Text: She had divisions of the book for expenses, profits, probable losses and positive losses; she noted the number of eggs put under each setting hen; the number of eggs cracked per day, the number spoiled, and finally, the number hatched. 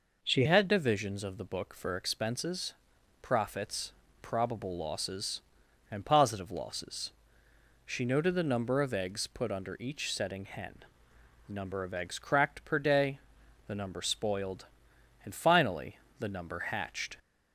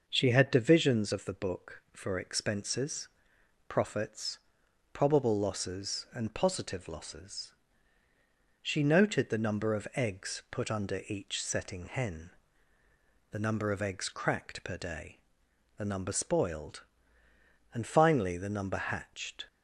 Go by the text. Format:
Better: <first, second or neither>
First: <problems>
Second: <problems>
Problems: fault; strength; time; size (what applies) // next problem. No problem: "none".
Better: second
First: changes voice at "had"; from 0.4 s on; 16.7 s long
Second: none